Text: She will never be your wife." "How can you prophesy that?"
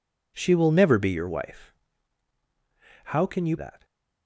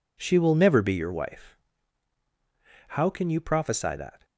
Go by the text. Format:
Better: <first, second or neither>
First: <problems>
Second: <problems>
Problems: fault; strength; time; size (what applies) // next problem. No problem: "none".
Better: second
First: skips "prophesy"; at 3.5 s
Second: none